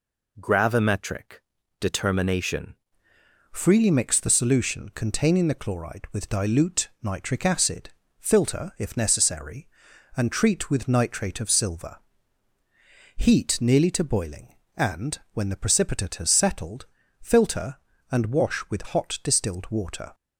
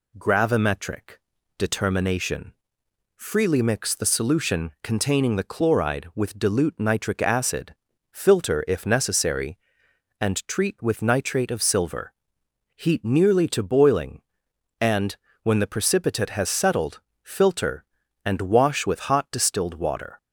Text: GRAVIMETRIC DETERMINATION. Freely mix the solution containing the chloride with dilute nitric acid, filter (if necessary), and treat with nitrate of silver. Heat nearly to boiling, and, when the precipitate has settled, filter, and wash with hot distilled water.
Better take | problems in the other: second | pauses between "GRAVIMETRIC" and "DETERMINATION"; slight; at 1.4 s; 0.36 s long; slight in the second // changes voice at "Freely"; from 3.5 s on; 16.6 s long

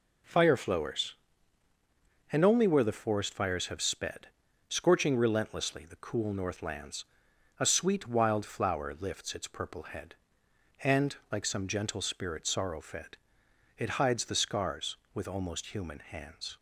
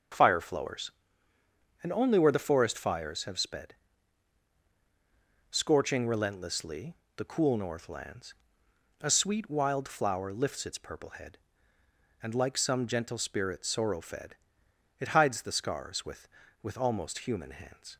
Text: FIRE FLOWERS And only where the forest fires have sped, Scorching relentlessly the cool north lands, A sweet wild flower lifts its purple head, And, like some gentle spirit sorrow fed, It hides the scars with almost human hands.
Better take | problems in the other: first | starts louder than the rest; until 2.0 s; 6.5 dB // pauses between "relentlessly" and "the"; slight; at 6.9 s; 0.22 s long // says "with" twice; at 16.6 s

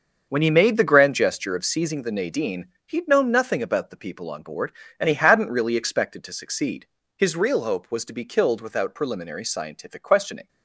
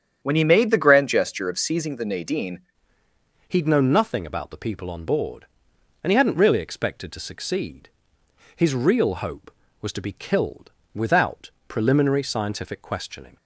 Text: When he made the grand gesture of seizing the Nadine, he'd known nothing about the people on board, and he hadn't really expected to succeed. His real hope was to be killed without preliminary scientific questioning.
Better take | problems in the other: first | starts louder than the rest; strong; until 1.2 s; 8.5 dB; also in the first // changes voice at "he'd"; from 3.4 s on; 9.9 s long // pauses between "killed" and "without"; slight; at 10.7 s; 0.24 s long // pauses between "without" and "preliminary"; slight; at 11.5 s; 0.18 s long

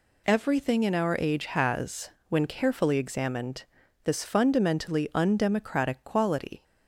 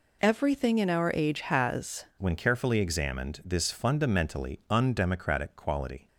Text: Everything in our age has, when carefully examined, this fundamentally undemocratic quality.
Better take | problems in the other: first | changes voice at "when"; from 2.1 s on; 3.9 s long

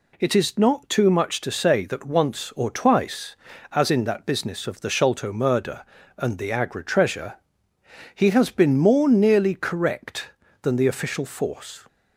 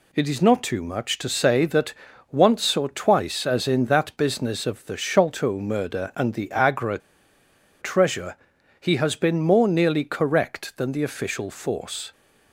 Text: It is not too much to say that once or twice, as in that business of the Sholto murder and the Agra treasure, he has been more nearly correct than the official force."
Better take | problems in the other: first | pauses between "that" and "once"; slight; at 1.9 s; 0.36 s long // pauses between "Agra" and "treasure"; noticeable; at 6.9 s; 0.82 s long

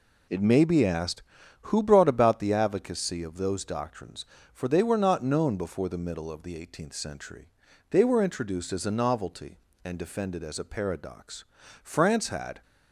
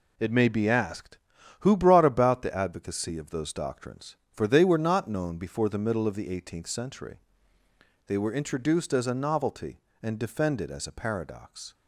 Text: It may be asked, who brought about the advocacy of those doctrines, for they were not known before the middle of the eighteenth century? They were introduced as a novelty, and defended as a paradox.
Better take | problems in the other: second | goes on to say "France had"; noticeable; from 11.8 s on; 0.78 s long

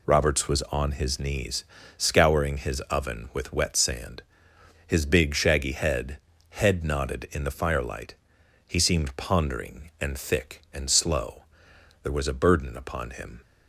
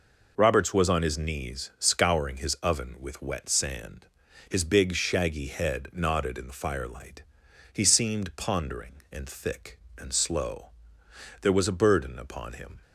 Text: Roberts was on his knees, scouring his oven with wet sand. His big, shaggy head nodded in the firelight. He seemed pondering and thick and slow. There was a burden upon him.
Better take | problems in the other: second | says "head" twice; at 6.5 s

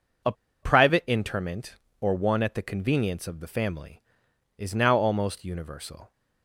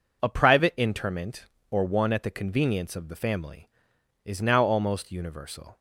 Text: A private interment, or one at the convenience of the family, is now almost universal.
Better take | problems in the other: second | pauses between "A" and "private"; slight; at 0.3 s; 0.29 s long

